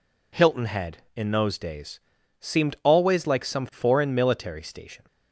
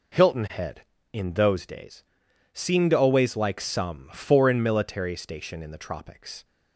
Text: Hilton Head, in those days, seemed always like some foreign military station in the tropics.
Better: second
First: stops before "in the tropics"; at 5.0 s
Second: none

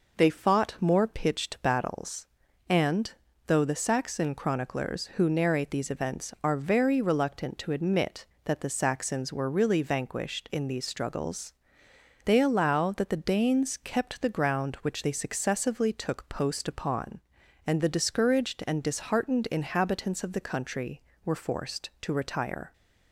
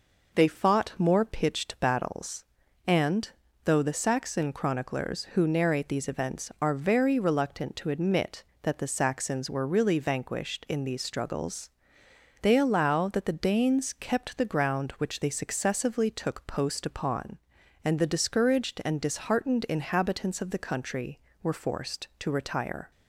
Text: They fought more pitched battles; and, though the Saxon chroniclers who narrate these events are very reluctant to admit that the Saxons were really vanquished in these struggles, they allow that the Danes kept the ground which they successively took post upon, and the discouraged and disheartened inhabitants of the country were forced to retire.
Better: neither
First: none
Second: none

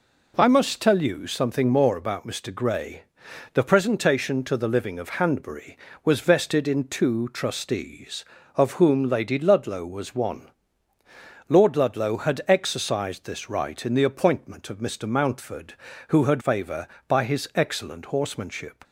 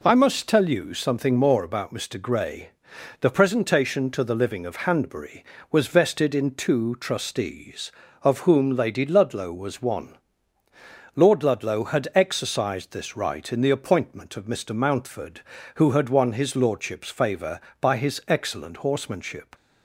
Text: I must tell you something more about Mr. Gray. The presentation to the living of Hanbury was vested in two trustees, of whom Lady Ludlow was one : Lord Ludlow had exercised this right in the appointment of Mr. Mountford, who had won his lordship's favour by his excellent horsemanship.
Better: second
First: skips "won his lordship's"; at 16.4 s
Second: none

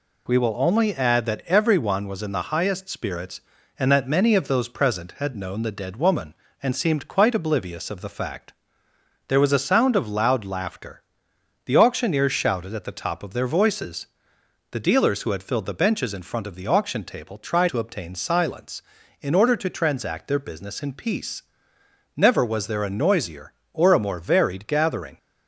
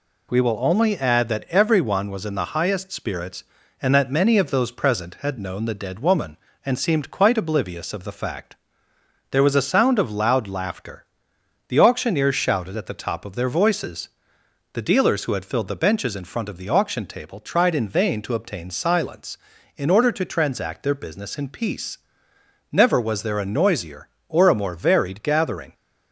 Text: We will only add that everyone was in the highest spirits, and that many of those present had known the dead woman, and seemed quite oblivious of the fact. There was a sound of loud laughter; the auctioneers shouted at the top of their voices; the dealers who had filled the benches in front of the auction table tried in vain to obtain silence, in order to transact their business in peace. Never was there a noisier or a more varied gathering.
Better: second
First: skips "in vain"; at 17.6 s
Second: none

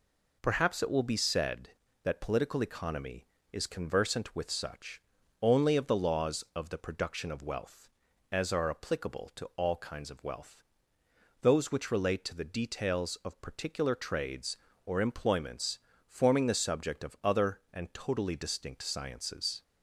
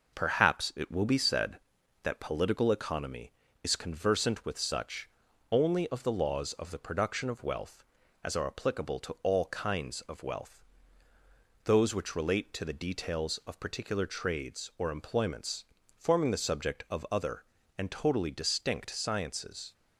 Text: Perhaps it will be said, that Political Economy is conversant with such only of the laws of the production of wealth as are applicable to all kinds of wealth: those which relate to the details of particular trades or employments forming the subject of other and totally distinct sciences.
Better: neither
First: pauses between "such" and "only"; at 5.0 s; 0.40 s long // pauses between "employments" and "forming"; slight; at 15.8 s; 0.26 s long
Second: pauses between "such" and "only"; at 5.0 s; 0.42 s long // pauses between "employments" and "forming"; slight; at 15.6 s; 0.32 s long

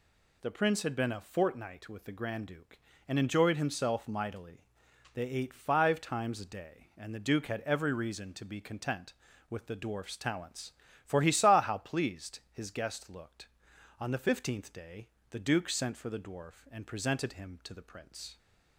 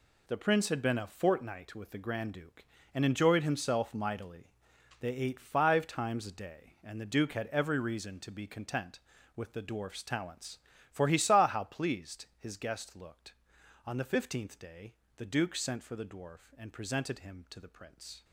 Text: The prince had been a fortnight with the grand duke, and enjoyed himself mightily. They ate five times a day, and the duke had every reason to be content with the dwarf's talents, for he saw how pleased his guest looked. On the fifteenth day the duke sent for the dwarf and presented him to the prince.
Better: first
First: pauses between "day" and "the"; slight; at 15.0 s; 0.22 s long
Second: gets quieter; strong; throughout; 9.5 dB // pauses between "day" and "the"; slight; at 14.9 s; 0.22 s long

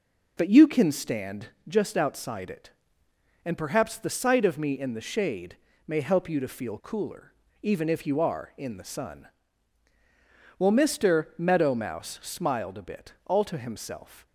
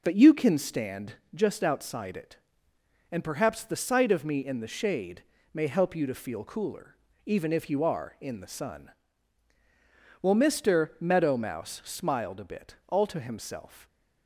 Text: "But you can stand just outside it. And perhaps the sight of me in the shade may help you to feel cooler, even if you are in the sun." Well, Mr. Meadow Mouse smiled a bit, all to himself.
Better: neither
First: pauses between "stand" and "just"; slight; at 1.4 s; 0.18 s long // pauses between "shade" and "may"; slight; at 5.5 s; 0.30 s long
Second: pauses between "stand" and "just"; slight; at 1.1 s; 0.18 s long // pauses between "shade" and "may"; slight; at 5.2 s; 0.30 s long

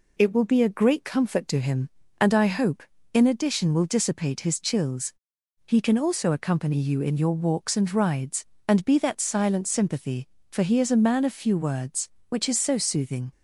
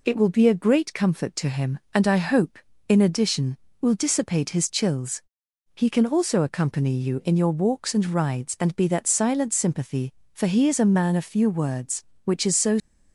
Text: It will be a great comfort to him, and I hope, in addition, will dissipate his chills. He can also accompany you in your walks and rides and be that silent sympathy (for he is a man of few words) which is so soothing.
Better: first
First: none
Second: stops before "soothing"; at 12.7 s

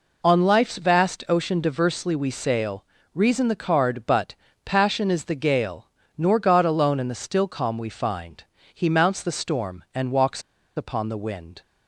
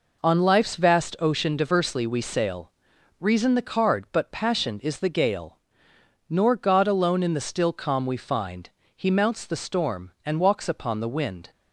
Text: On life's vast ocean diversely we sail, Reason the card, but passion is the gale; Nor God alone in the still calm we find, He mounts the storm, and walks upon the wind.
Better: second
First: pauses between "but" and "passion"; slight; at 4.3 s; 0.30 s long // pauses between "walks" and "upon"; slight; at 10.4 s; 0.35 s long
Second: none

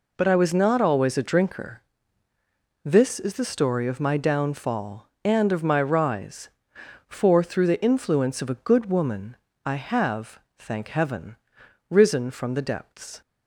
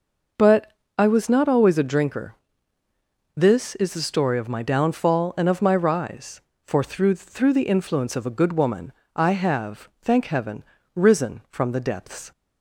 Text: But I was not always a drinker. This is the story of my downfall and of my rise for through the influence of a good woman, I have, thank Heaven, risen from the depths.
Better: first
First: none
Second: pauses between "But" and "I"; slight; at 0.7 s; 0.26 s long // says "through" twice; at 7.1 s

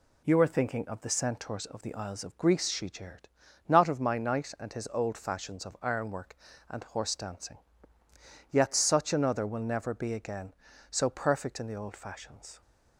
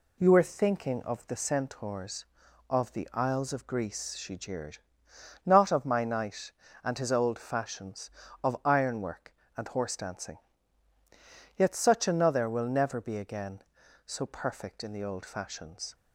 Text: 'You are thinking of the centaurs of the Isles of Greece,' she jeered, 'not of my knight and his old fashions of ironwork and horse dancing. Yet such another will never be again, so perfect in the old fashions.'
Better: neither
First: none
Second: none

